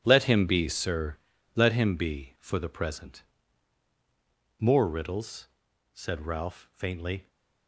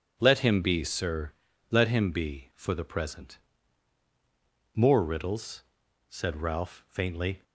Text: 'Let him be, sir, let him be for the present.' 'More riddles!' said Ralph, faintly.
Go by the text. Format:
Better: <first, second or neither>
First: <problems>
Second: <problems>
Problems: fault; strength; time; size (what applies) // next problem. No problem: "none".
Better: second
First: gets quieter; strong; throughout; 12 dB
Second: none